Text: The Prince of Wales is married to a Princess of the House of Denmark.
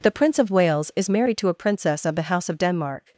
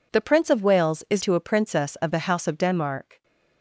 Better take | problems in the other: first | skips "married"; at 1.2 s

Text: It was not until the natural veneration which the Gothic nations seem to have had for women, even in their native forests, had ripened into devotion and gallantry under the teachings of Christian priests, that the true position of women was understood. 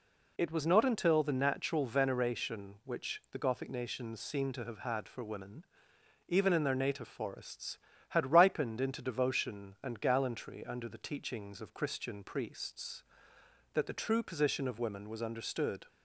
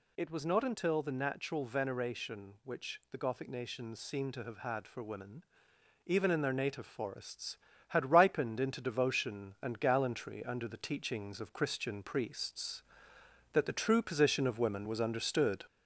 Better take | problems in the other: first | gets louder; slight; throughout; 3 dB

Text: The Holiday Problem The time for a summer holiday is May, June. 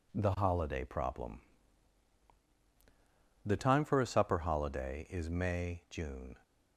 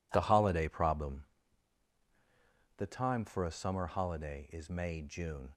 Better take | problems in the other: second | pauses between "Problem" and "The"; strong; at 1.3 s; 2.0 s long; strong in the second // says "supper" for "summer"; at 4.0 s

